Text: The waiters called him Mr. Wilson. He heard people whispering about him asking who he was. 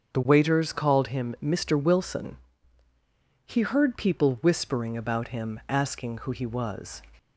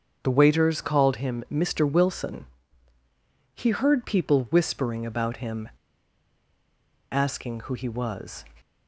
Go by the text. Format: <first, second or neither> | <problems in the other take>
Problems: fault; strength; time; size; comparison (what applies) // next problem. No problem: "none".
first | starts louder than the rest; strong; until 1.2 s; 7 dB; strong in the first // pauses between "him" and "asking"; strong; at 5.6 s; 1.4 s long